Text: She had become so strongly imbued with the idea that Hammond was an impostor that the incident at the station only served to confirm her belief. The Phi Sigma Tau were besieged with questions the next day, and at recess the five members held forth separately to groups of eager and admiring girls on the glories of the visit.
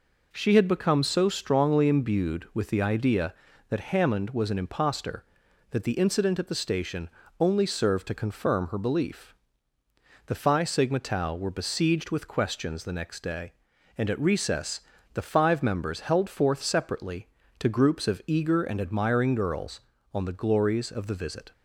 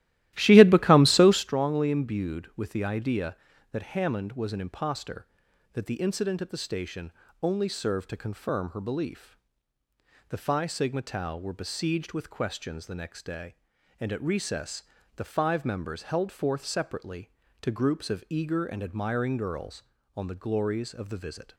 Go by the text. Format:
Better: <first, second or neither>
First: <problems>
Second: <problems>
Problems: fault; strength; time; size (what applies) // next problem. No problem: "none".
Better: first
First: pauses between "station" and "only"; slight; at 7.0 s; 0.30 s long // pauses between "recess" and "the"; slight; at 14.7 s; 0.34 s long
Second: starts louder than the rest; strong; until 1.5 s; 15 dB // pauses between "station" and "only"; slight; at 7.1 s; 0.30 s long // pauses between "recess" and "the"; slight; at 14.8 s; 0.34 s long